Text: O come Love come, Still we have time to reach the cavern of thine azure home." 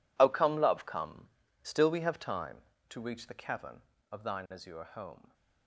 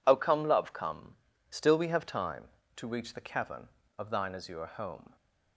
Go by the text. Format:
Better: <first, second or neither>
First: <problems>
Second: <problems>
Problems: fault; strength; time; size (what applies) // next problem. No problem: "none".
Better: second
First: gets quieter; strong; throughout; 16 dB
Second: none